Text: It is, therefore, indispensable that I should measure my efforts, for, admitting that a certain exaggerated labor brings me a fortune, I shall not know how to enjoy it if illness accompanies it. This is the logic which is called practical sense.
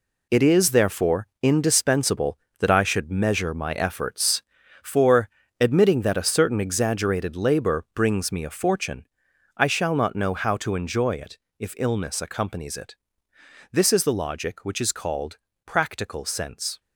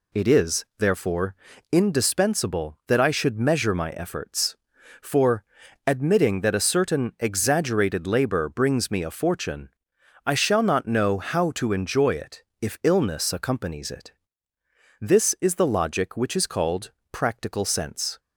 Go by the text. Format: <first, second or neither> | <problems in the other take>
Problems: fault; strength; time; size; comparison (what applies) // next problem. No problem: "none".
second | gets quieter; strong; throughout; 9.5 dB // pauses between "it" and "if"; slight; at 11.3 s; 0.20 s long; slight in the second // pauses between "called" and "practical"; slight; at 15.3 s; 0.28 s long; slight in the second